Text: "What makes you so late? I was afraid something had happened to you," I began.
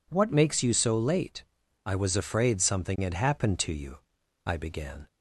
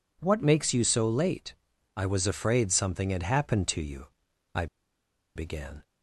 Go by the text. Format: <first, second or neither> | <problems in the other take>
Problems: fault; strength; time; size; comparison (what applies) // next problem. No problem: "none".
first | pauses between "I" and "began"; noticeable; at 4.6 s; 0.70 s long